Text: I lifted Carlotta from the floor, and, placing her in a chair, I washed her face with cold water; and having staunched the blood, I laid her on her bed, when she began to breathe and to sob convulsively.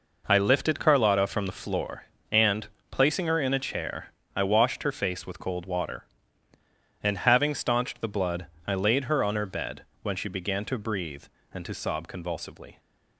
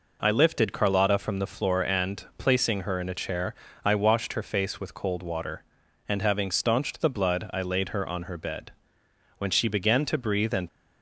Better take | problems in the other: first | stops before "to sob convulsively"; at 10.6 s

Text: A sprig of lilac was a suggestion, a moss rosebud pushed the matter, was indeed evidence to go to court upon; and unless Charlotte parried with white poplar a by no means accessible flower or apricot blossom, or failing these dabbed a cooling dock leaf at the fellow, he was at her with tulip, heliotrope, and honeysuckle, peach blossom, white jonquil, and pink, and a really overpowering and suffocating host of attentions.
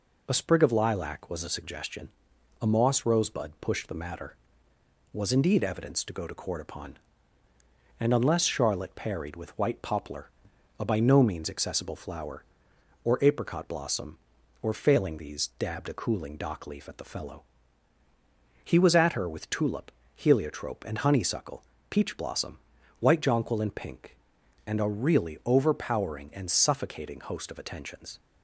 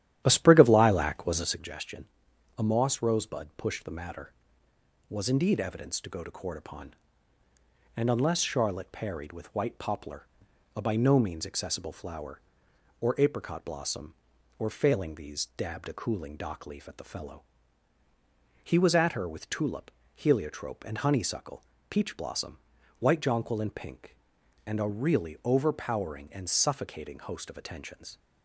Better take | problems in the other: first | starts louder than the rest; strong; until 1.7 s; 12 dB // pauses between "poplar" and "a"; noticeable; at 10.2 s; 0.48 s long; noticeable in the first

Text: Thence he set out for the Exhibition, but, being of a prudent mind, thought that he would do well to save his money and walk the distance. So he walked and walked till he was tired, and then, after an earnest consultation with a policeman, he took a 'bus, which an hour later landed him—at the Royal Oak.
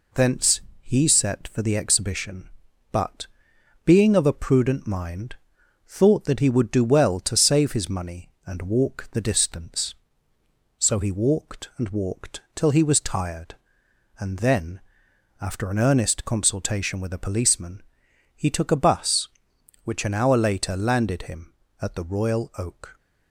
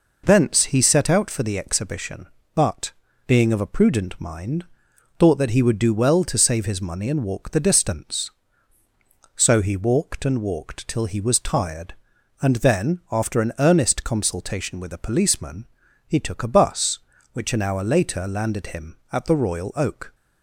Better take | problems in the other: second | pauses between "Thence" and "he"; slight; at 0.5 s; 0.20 s long // skips "out"; at 1.4 s

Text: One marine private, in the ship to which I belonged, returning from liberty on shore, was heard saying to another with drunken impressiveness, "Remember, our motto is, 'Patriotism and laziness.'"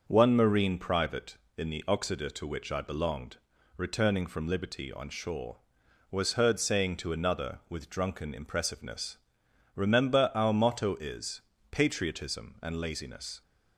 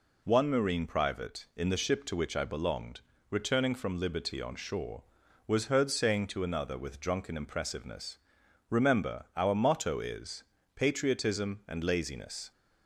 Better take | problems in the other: second | starts louder than the rest; until 1.0 s; 6.5 dB // says "oxida" for "ship"; at 1.8 s

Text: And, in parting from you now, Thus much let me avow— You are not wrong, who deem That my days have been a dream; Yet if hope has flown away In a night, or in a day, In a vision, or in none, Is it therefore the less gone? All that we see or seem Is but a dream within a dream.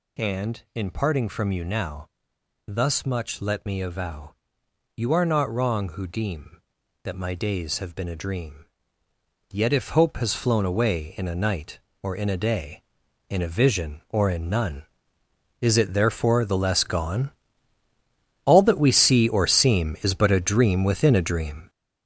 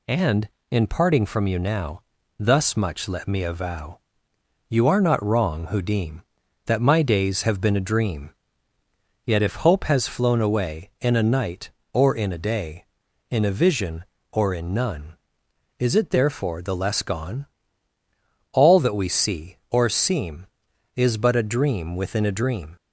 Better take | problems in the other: second | gets louder; strong; throughout; 8 dB

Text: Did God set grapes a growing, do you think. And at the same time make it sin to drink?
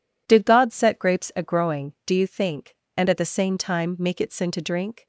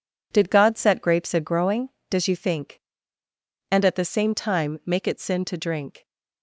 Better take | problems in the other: first | says "does" for "do"; at 2.0 s

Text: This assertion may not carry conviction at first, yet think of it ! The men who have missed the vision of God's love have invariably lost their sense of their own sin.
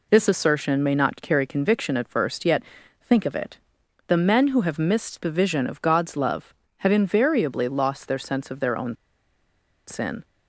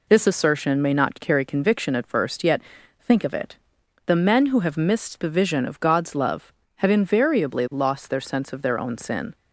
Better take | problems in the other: second | pauses between "yet" and "think"; at 2.6 s; 0.40 s long; also in the second // pauses between "own" and "sin"; noticeable; at 8.9 s; 0.92 s long

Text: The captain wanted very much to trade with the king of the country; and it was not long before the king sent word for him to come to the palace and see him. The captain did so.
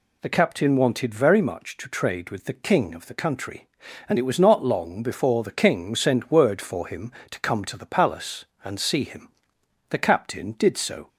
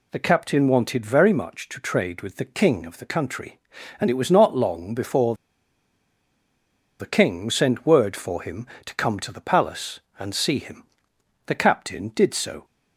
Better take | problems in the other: first | pauses between "before" and "the"; strong; at 5.3 s; 1.6 s long

